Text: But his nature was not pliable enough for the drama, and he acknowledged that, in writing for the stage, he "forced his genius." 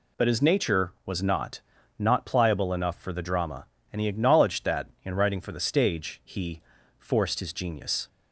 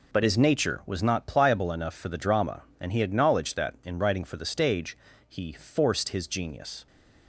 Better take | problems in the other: second | says "not" twice; at 1.9 s // pauses between "he" and "forced"; at 6.5 s; 0.38 s long

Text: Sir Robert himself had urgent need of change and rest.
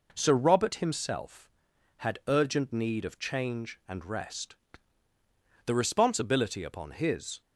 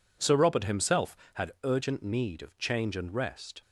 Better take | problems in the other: second | goes on to say "The responsibility upon his"; strong; from 5.6 s on; 1.7 s long

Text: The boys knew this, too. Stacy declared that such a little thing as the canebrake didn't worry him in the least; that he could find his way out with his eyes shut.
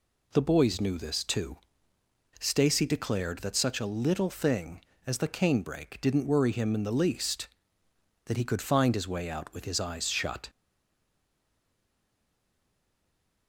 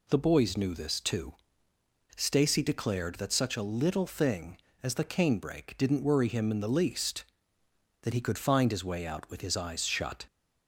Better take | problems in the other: second | stays silent after the last word; strong; from 10.4 s on; 3.0 s long

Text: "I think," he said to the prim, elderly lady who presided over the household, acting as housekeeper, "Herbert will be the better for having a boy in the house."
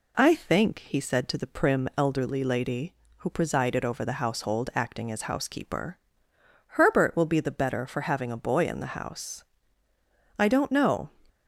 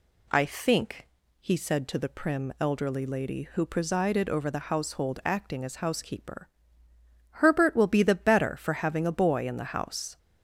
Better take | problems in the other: second | goes on to say "I don't know"; noticeable; from 10.3 s on; 0.72 s long

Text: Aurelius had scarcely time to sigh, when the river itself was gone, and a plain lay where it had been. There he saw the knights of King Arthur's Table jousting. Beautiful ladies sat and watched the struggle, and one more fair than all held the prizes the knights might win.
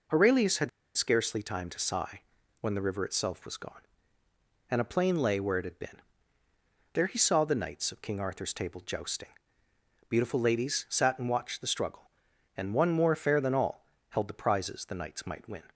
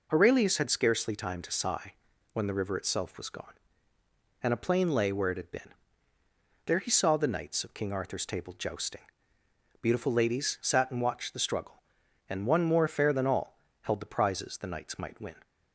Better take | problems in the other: second | pauses between "had" and "scarcely"; slight; at 0.6 s; 0.26 s long // pauses between "all" and "held"; slight; at 13.8 s; 0.26 s long; slight in the second

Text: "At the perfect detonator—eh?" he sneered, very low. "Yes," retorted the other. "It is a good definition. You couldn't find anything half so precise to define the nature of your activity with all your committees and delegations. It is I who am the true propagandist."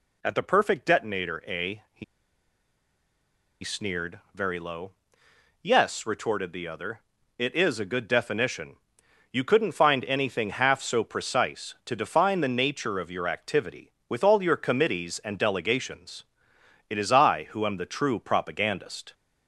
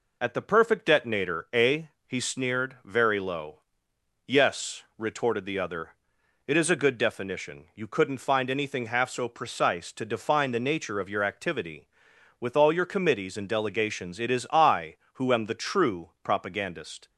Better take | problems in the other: second | pauses between "he" and "sneered"; strong; at 2.0 s; 1.5 s long

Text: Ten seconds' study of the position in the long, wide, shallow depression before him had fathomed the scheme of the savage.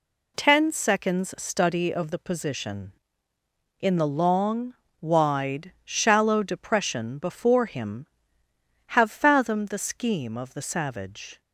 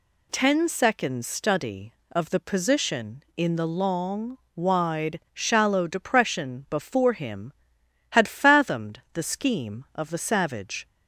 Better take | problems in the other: second | says "have" for "had"; at 8.8 s

